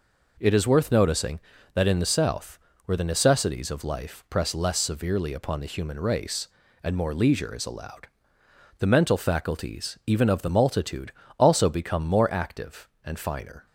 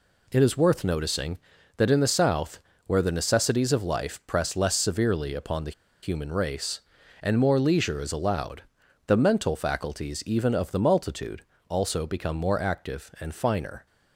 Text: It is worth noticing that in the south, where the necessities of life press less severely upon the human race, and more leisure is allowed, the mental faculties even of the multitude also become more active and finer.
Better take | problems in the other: first | pauses between "the" and "human"; slight; at 5.7 s; 0.31 s long // pauses between "multitude" and "also"; slight; at 11.4 s; 0.26 s long; slight in the first

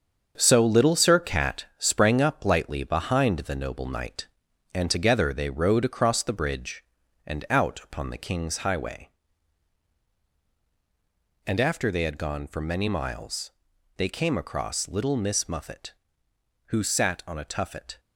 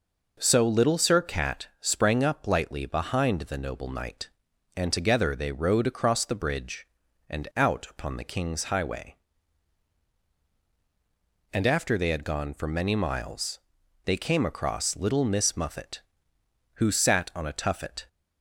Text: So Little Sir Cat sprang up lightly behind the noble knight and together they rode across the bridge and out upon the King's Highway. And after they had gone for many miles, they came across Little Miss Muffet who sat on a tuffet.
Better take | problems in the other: second | gets quieter; strong; throughout; 7.5 dB

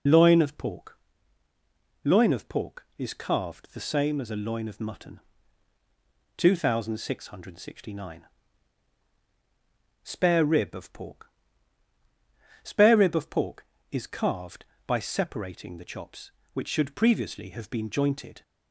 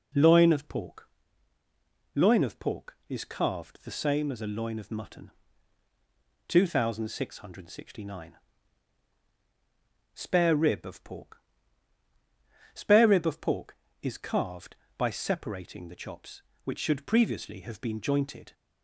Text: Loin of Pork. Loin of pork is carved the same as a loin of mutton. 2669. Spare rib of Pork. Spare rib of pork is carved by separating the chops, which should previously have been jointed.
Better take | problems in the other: second | loses the start of "Loin"; at 0.0 s; 30 ms

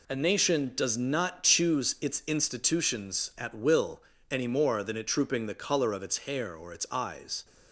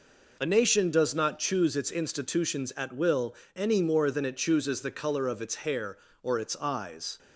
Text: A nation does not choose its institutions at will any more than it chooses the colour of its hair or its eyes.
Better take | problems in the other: second | pauses between "will" and "any"; slight; at 4.0 s; 0.26 s long; slight in the second // says "trooping" for "chooses"; at 5.0 s

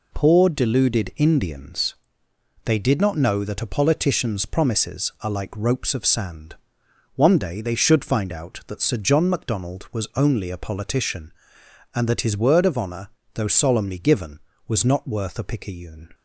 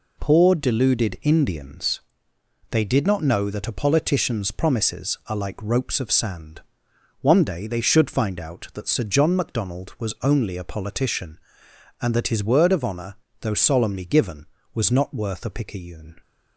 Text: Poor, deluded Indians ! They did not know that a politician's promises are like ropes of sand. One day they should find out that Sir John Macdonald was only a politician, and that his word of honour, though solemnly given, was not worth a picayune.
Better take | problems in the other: neither | none

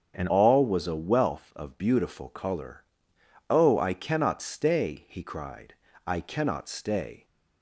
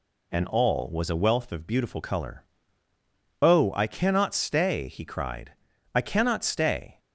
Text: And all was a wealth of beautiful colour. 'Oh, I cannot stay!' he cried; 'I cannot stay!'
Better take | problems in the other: second | starts louder than the rest; strong; until 1.2 s; 8 dB // changes voice at "all"; from 0.2 s on; 7.0 s long

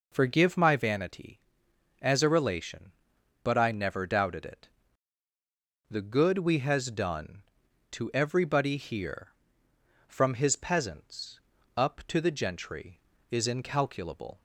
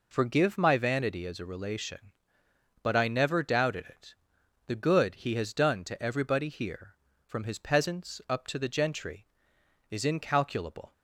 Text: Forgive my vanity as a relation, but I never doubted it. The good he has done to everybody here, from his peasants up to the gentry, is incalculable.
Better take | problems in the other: second | says "we" for "he"; at 6.3 s // pauses between "peasants" and "up"; slight; at 11.3 s; 0.36 s long

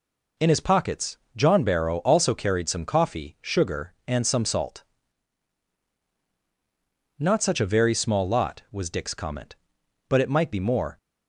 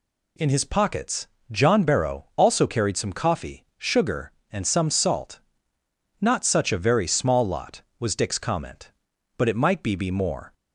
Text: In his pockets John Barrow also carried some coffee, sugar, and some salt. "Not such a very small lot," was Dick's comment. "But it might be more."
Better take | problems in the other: first | pauses between "pockets" and "John"; slight; at 1.2 s; 0.22 s long; slight in the first // says "be" twice; at 9.9 s

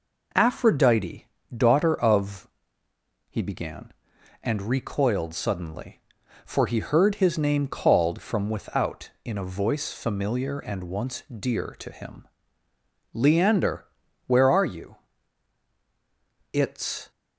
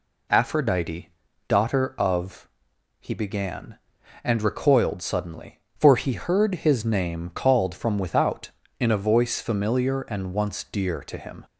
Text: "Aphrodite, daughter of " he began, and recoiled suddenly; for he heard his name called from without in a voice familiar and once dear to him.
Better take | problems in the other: second | goes on to say "Leander where are you It's"; strong; from 13.1 s on; 3.9 s long

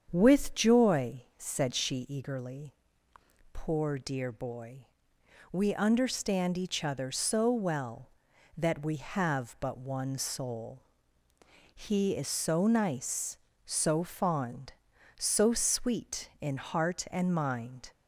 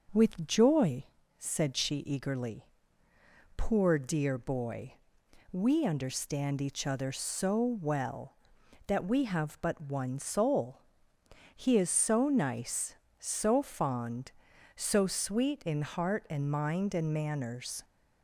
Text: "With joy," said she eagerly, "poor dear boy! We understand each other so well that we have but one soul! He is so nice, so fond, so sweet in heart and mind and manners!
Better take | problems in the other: second | starts louder than the rest; strong; until 1.1 s; 7.5 dB // stops before "and manners"; at 17.9 s

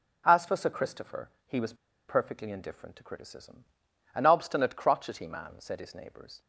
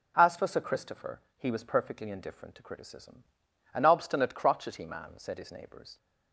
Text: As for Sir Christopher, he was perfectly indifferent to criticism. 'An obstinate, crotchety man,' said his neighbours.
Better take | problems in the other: second | pauses between "was" and "perfectly"; slight; at 1.7 s; 0.33 s long

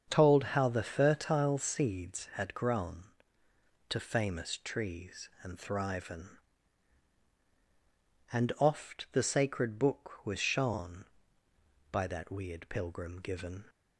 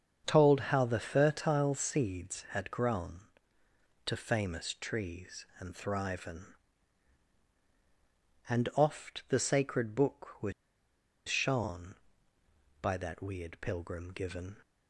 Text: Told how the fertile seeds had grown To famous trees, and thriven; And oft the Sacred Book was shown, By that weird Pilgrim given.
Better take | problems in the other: first | starts louder than the rest; strong; until 1.3 s; 7 dB; also in the first // pauses between "was" and "shown"; noticeable; at 10.5 s; 0.76 s long

